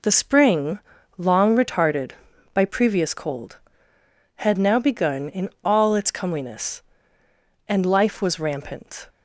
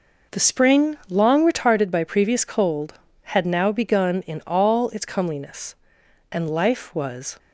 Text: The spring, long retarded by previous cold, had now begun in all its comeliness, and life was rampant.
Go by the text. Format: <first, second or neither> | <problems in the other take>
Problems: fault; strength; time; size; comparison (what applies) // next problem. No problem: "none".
first | stops before "rampant"; at 7.3 s